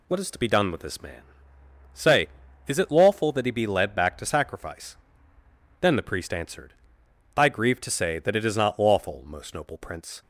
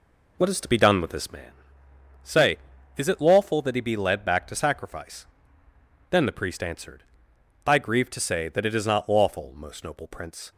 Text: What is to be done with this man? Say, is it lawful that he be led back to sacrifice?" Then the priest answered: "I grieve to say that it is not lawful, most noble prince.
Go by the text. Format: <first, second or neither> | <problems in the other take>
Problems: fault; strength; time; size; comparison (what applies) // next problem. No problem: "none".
first | starts louder than the rest; until 1.3 s; 3.5 dB